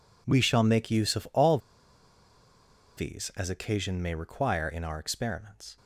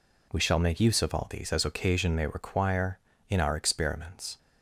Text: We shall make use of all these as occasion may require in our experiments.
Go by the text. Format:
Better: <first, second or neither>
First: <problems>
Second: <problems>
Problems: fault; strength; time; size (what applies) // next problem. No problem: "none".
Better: second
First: pauses between "all" and "these"; strong; at 1.5 s; 1.3 s long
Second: none